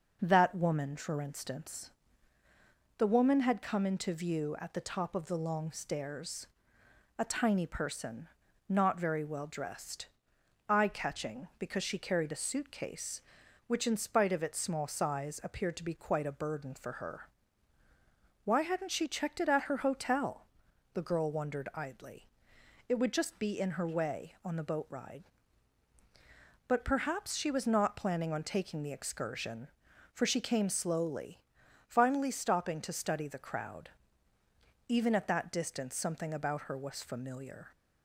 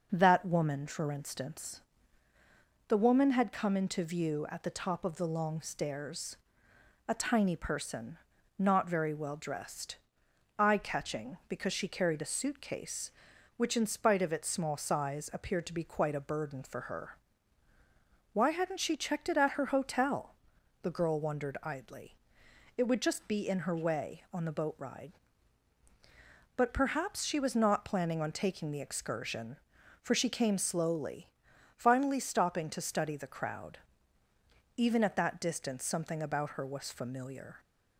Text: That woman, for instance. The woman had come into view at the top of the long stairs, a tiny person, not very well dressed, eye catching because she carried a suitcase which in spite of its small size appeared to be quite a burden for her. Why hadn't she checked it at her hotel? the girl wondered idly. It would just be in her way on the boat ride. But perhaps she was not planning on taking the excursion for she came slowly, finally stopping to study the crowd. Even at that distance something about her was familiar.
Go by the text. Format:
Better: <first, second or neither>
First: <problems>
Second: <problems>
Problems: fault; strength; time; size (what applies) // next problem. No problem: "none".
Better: neither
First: none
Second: none